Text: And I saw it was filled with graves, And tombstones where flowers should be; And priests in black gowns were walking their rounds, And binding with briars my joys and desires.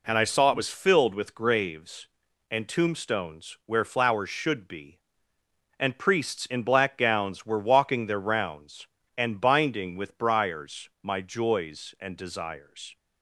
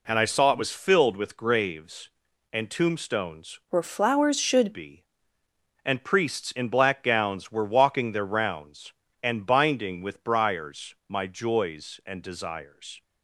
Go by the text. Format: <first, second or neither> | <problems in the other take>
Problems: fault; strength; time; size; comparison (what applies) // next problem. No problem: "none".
first | changes voice from "where" to "should"; from 3.6 to 4.7 s; 1.1 s long